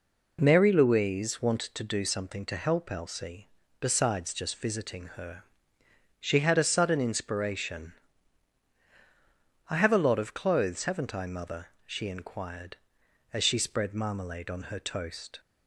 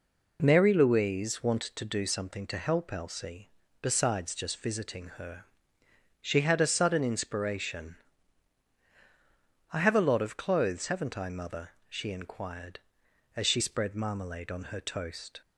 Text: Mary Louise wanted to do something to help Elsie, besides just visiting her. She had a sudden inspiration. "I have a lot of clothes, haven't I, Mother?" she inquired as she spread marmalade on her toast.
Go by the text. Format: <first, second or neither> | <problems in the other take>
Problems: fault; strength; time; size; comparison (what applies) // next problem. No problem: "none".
neither | none